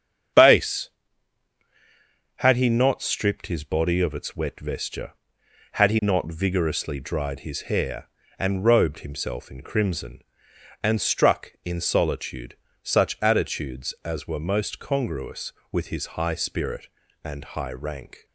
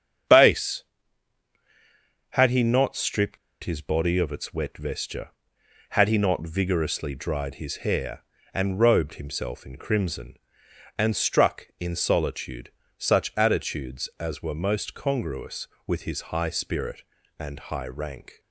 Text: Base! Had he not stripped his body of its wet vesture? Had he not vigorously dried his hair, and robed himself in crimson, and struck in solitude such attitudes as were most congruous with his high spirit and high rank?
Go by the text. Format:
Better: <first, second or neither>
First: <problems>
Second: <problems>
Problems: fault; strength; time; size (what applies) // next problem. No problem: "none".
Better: first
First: starts louder than the rest; strong; until 2.8 s; 8 dB // pauses between "solitude" and "such"; slight; at 12.5 s; 0.28 s long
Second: starts louder than the rest; strong; until 2.7 s; 8 dB // pauses between "stripped" and "his"; slight; at 3.3 s; 0.26 s long // pauses between "solitude" and "such"; slight; at 12.7 s; 0.28 s long